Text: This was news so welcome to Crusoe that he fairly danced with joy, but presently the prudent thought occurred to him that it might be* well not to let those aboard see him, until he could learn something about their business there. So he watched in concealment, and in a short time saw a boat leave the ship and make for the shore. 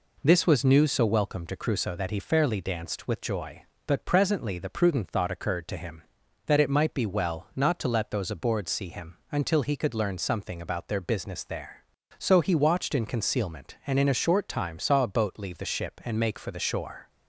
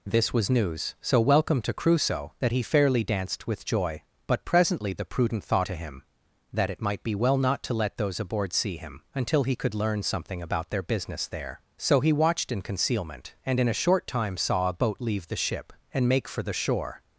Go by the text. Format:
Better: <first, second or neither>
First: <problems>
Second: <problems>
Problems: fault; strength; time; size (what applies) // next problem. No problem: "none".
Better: first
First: none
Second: skips "occurred"; at 5.6 s